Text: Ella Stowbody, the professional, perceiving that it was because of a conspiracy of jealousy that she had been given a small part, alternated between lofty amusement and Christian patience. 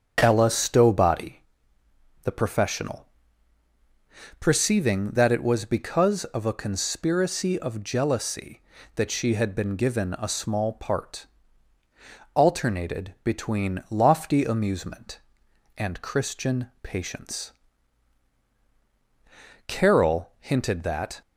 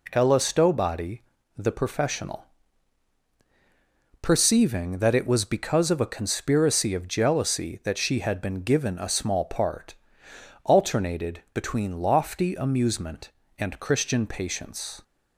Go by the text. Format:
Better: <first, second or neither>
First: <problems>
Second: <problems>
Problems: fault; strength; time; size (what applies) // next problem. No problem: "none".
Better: second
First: starts louder than the rest; strong; until 1.2 s; 7.5 dB // goes on to say "Carol hinted that"; from 19.6 s on; 1.5 s long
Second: none